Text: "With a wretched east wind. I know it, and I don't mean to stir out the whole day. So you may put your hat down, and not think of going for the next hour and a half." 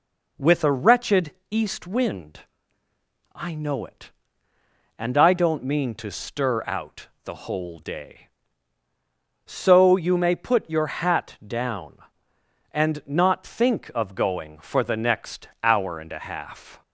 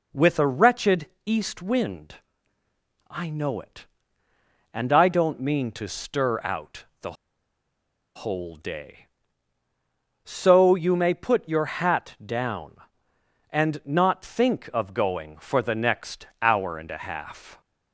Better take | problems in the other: first | pauses between "wretched" and "east"; slight; at 1.0 s; 0.18 s long; slight in the first // pauses between "out" and "the"; slight; at 6.8 s; 0.18 s long; slight in the first // pauses between "the" and "whole"; at 7.1 s; 1.0 s long

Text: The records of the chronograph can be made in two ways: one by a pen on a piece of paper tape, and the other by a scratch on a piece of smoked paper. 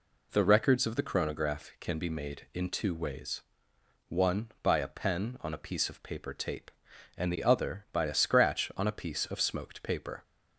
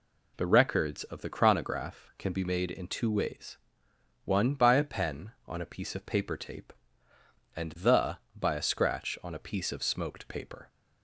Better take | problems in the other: first | skips "other"; at 8.2 s

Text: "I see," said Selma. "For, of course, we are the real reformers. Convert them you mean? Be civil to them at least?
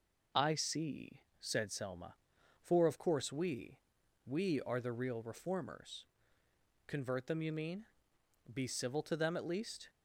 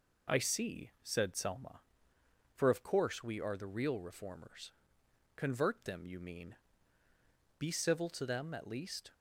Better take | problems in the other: second | says "we" twice; at 4.2 s

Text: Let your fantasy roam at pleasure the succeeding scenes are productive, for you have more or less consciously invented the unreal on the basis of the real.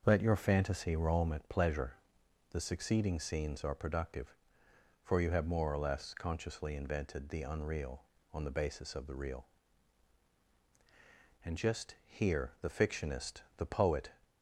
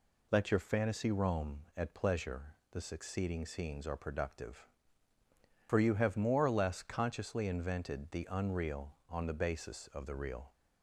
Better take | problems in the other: second | starts louder than the rest; until 1.0 s; 6.5 dB // pauses between "pleasure" and "the"; noticeable; at 1.9 s; 0.56 s long; slight in the second // goes on to say "And just here the fictionist the poet"; strong; from 11.4 s on; 2.6 s long

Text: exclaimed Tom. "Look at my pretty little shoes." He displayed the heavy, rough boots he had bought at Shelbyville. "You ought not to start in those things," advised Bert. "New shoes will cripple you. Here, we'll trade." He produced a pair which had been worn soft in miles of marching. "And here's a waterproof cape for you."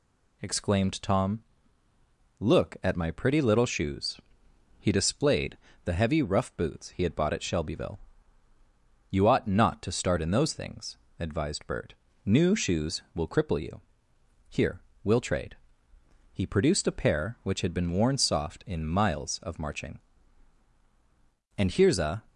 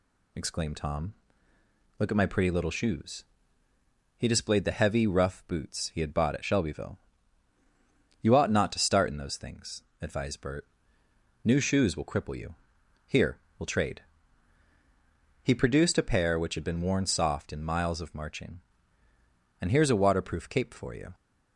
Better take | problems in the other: second | pauses between "displayed" and "the"; slight; at 5.5 s; 0.28 s long // stops before "waterproof cape for you"; at 22.2 s

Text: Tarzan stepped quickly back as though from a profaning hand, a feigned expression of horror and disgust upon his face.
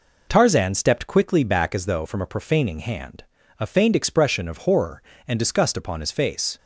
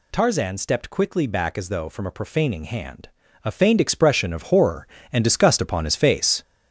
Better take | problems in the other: first | gets louder; throughout; 6.5 dB

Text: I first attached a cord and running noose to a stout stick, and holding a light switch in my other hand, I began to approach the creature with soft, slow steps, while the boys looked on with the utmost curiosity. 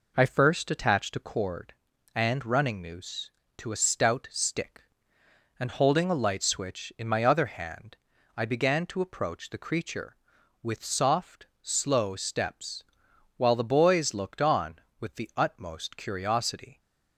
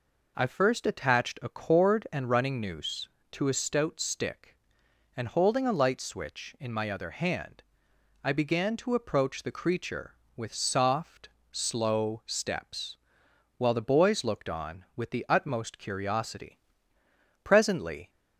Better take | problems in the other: first | goes on to say "Presently"; noticeable; from 17.4 s on; 0.66 s long

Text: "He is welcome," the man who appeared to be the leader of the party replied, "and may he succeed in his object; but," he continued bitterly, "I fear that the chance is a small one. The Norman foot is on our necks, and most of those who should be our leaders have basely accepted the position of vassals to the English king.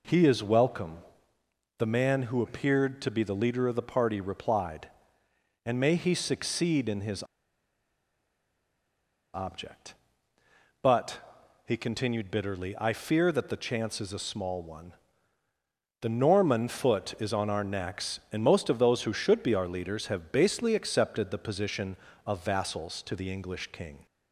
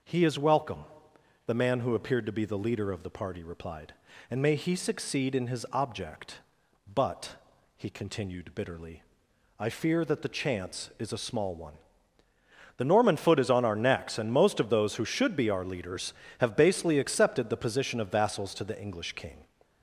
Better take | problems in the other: second | pauses between "his" and "object"; strong; at 7.2 s; 2.0 s long

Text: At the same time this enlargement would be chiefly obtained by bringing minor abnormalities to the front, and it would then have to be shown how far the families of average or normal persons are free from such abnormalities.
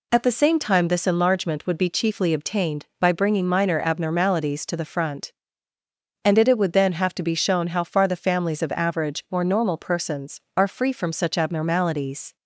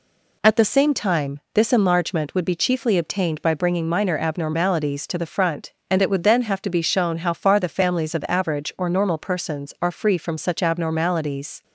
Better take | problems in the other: second | says "it" twice; at 6.4 s

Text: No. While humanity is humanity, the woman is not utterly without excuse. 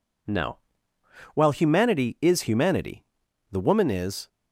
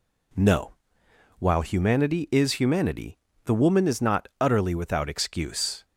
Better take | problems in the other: second | stops before "not utterly without excuse"; at 4.2 s

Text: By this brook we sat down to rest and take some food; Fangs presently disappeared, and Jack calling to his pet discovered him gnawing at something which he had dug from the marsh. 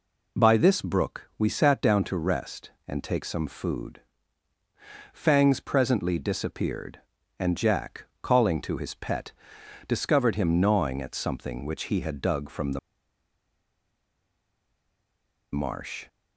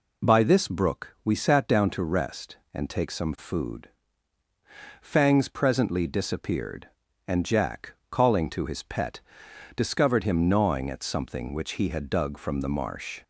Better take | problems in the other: second | pauses between "Jack" and "calling"; slight; at 8.0 s; 0.16 s long; slight in the second // pauses between "pet" and "discovered"; noticeable; at 9.3 s; 0.56 s long; noticeable in the second // pauses between "the" and "marsh"; strong; at 12.7 s; 2.7 s long

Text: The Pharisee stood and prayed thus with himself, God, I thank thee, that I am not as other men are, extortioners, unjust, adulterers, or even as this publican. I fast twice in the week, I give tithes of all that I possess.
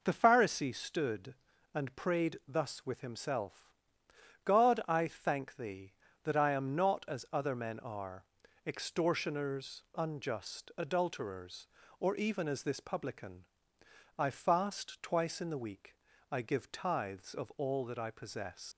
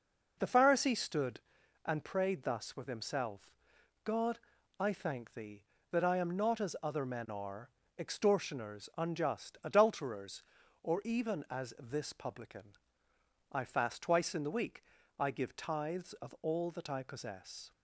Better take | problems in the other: second | leaves "possess" unfinished; at 18.7 s; 115 ms

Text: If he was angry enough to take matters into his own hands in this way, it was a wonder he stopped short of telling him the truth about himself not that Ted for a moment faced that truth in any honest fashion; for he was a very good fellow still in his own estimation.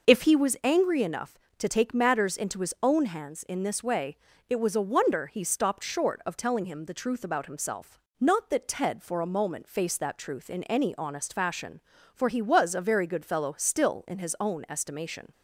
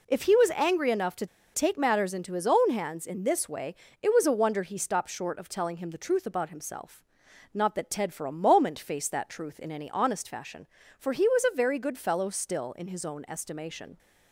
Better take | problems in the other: first | pauses between "to" and "take"; slight; at 1.2 s; 0.27 s long // pauses between "himself" and "not"; noticeable; at 7.0 s; 0.48 s long; slight in the first

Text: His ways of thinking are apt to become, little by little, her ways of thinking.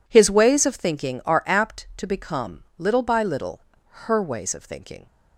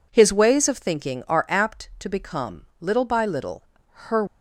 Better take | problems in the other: first | stops before "ways of thinking"; at 4.2 s

